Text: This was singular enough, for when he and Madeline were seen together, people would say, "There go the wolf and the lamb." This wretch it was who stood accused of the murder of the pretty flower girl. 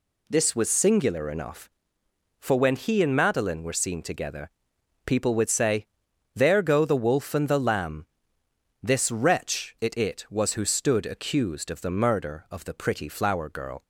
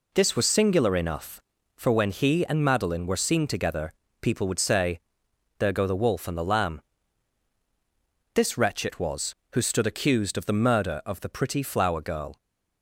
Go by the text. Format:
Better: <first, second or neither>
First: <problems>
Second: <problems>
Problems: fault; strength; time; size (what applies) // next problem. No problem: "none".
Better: second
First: says "it" twice; at 9.9 s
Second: none